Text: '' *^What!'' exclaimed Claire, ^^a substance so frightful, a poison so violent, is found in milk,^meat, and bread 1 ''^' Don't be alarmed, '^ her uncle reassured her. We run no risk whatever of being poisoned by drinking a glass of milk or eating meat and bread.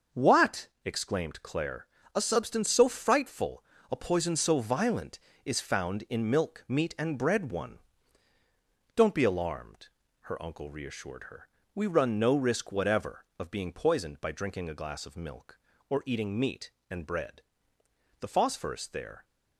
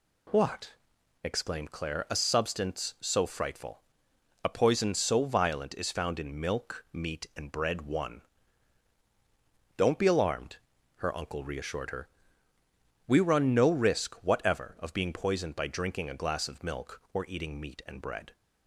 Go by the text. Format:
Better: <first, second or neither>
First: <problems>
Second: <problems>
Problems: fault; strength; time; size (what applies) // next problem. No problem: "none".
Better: second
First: starts louder than the rest; until 1.2 s; 6 dB // goes on to say "The phosphorus there"; noticeable; from 18.2 s on; 1.0 s long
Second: none